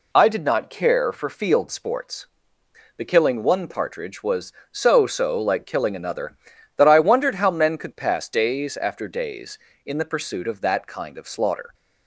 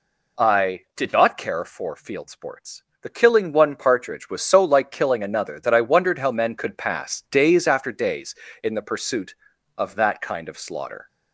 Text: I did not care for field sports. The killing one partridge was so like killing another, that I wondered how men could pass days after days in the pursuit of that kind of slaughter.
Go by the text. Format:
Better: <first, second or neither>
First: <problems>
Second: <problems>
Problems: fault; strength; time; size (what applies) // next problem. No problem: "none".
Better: second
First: says "so" twice; at 5.0 s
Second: none